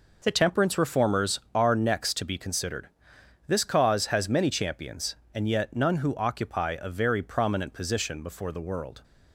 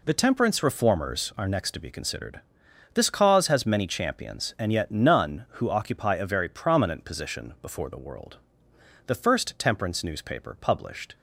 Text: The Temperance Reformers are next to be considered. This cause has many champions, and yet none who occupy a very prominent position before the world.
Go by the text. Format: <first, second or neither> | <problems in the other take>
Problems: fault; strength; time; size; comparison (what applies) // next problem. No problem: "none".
first | goes on to say "The first temperance newspaper published"; strong; from 9.0 s on; 2.0 s long